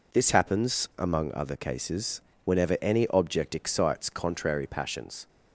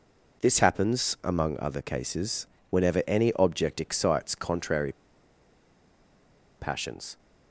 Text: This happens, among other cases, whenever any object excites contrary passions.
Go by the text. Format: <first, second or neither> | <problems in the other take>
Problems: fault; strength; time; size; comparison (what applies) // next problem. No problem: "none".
first | pauses between "contrary" and "passions"; strong; at 4.9 s; 1.6 s long